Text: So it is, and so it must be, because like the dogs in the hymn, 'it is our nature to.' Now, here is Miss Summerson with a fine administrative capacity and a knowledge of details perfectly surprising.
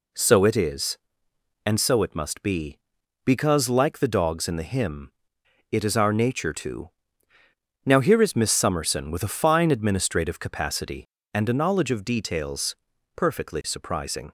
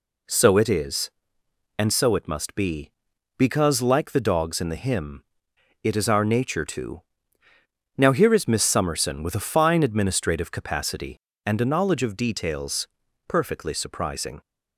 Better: neither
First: pauses between "details" and "perfectly"; at 12.7 s; 0.40 s long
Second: pauses between "details" and "perfectly"; at 12.8 s; 0.40 s long

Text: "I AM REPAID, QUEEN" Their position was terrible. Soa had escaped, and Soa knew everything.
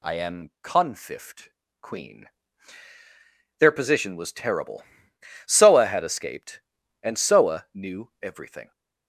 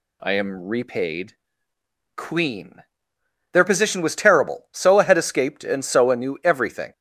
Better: second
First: says "Confift" for "REPAID"; at 0.6 s // pauses between "QUEEN" and "Their"; strong; at 2.2 s; 1.3 s long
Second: pauses between "QUEEN" and "Their"; noticeable; at 2.8 s; 0.70 s long

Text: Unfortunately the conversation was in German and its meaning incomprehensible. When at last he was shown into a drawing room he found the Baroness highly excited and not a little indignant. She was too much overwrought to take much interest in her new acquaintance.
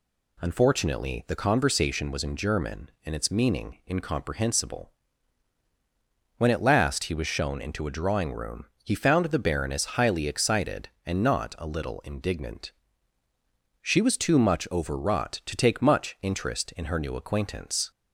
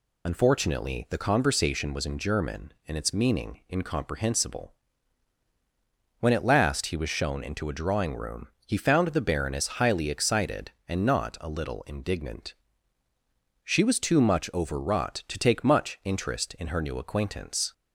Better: first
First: pauses between "room" and "he"; slight; at 8.6 s; 0.18 s long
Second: loses the start of "Unfortunately"; at 0.2 s; 55 ms // pauses between "room" and "he"; slight; at 8.4 s; 0.18 s long

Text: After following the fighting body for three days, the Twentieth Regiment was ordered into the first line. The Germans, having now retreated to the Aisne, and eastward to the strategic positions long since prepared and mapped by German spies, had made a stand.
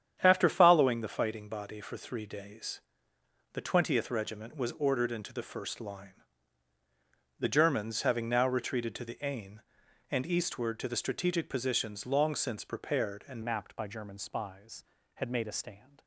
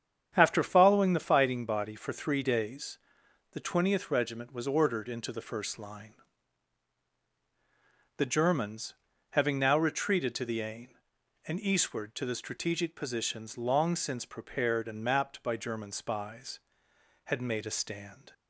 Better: second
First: starts louder than the rest; strong; until 1.2 s; 9 dB // changes voice at "mapped"; from 13.4 s on; 2.6 s long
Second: starts louder than the rest; strong; until 1.3 s; 8.5 dB

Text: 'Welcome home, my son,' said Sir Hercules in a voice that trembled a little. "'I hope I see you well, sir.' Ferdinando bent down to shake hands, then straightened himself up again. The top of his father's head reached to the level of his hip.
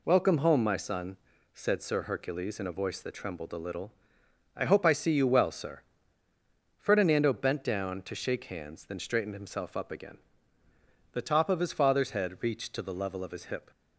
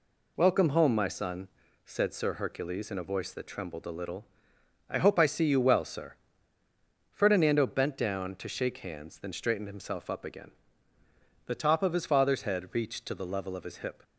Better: neither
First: none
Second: none

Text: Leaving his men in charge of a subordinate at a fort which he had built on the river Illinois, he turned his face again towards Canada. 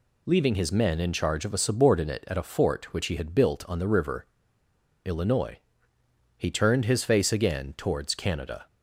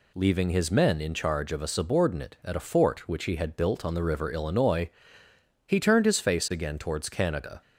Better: second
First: pauses between "river" and "Illinois"; noticeable; at 4.2 s; 0.77 s long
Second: none

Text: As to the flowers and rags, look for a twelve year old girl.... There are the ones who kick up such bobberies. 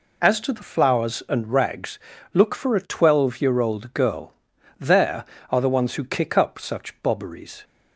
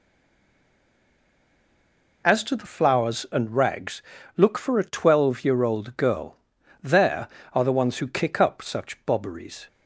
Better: first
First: none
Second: stays silent before the first word; until 2.2 s; 2.2 s long

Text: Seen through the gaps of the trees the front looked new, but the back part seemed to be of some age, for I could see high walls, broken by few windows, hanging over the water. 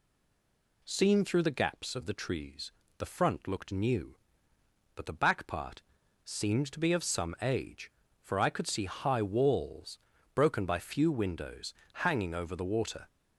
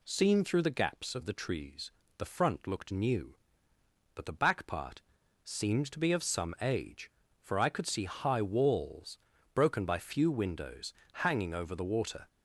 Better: second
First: stays silent before the first word; slight; until 0.8 s; 0.8 s long // pauses between "trees" and "the"; slight; at 2.7 s; 0.26 s long // pauses between "part" and "seemed"; at 5.8 s; 0.42 s long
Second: pauses between "trees" and "the"; slight; at 1.9 s; 0.26 s long // pauses between "part" and "seemed"; at 5.0 s; 0.42 s long

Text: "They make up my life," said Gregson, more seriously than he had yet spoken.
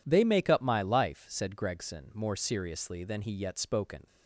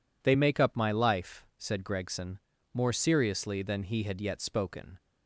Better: second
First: skips "had"; at 3.3 s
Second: none

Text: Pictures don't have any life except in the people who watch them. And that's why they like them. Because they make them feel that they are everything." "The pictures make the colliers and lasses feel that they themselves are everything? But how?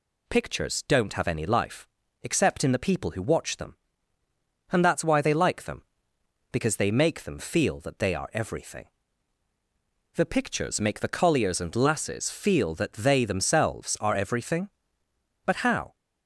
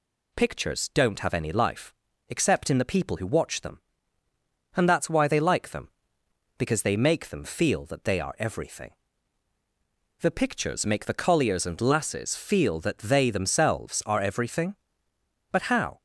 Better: neither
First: pauses between "life" and "except"; slight; at 1.8 s; 0.36 s long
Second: pauses between "life" and "except"; slight; at 1.9 s; 0.36 s long

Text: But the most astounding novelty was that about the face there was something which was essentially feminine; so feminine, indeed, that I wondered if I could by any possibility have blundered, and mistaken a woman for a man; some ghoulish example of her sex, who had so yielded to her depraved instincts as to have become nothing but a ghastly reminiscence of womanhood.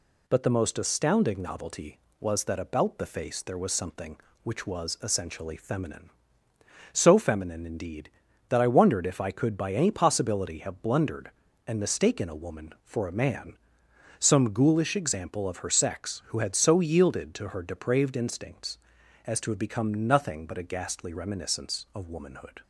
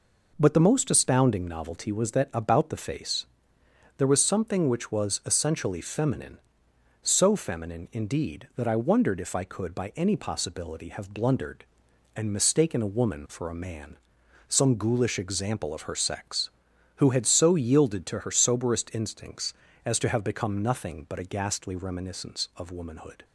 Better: first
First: none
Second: pauses between "face" and "there"; noticeable; at 3.2 s; 0.72 s long // says "soberest" for "depraved"; at 18.3 s

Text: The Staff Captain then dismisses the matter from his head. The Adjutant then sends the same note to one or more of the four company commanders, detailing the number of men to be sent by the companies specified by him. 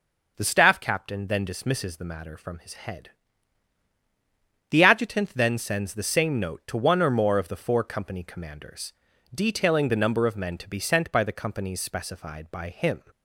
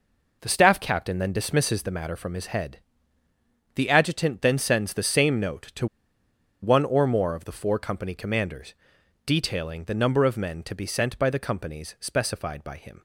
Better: first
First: none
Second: pauses between "to" and "one"; noticeable; at 5.8 s; 0.75 s long

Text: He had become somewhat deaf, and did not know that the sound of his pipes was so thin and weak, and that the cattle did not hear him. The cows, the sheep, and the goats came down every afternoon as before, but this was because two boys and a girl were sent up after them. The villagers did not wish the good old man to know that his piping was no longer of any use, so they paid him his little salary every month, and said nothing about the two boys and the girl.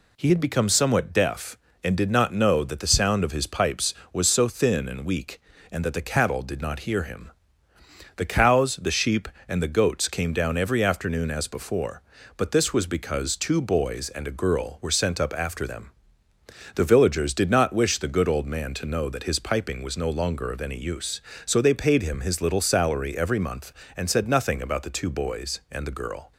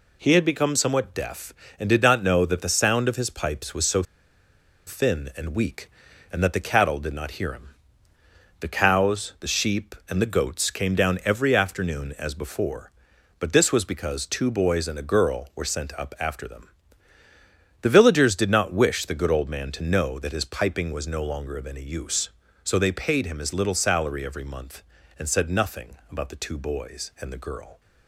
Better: first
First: none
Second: pauses between "so" and "thin"; noticeable; at 4.0 s; 0.84 s long // pauses between "nothing" and "about"; slight; at 25.9 s; 0.16 s long

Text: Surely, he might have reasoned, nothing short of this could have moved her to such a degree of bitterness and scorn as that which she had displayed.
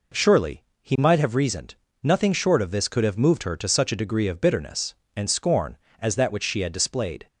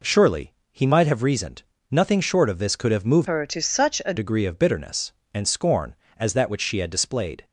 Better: first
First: none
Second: changes voice from "her" to "a"; from 3.2 to 4.1 s; 0.9 s long

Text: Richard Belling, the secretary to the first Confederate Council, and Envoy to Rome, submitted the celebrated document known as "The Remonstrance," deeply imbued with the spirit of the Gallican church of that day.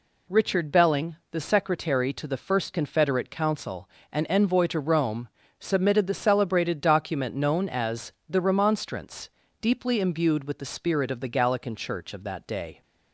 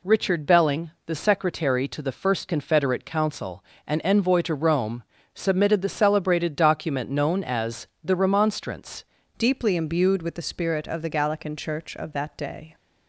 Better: first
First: pauses between "as" and "The"; slight; at 8.1 s; 0.16 s long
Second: pauses between "as" and "The"; slight; at 7.8 s; 0.16 s long // changes voice at "deeply"; from 9.3 s on; 3.4 s long

